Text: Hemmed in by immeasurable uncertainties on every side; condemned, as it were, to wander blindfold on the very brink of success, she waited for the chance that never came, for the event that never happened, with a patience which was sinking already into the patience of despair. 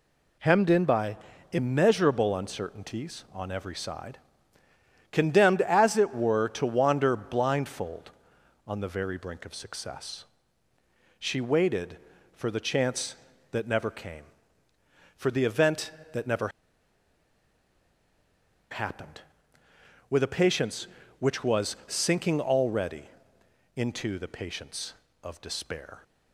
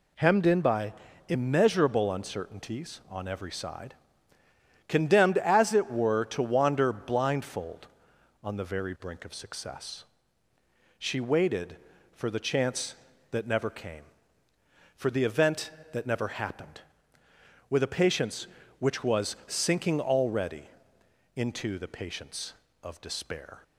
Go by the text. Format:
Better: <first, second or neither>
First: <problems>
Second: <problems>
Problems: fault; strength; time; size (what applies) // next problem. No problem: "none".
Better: second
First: pauses between "by" and "immeasurable"; slight; at 1.1 s; 0.34 s long // pauses between "never" and "happened"; strong; at 16.4 s; 2.2 s long // pauses between "already" and "into"; noticeable; at 23.0 s; 0.72 s long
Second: pauses between "by" and "immeasurable"; slight; at 0.9 s; 0.34 s long // pauses between "already" and "into"; noticeable; at 20.6 s; 0.72 s long